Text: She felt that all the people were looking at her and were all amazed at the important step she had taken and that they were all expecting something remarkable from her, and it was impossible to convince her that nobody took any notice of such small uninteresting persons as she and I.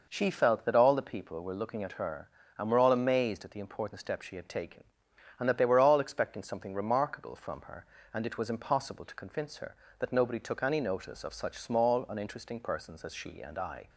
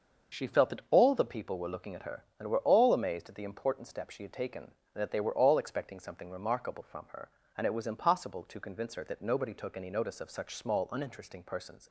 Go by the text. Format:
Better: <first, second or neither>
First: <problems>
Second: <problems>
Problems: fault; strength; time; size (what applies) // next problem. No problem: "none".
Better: first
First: none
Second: starts louder than the rest; until 1.4 s; 6.5 dB // stops before "as she and I"; at 11.8 s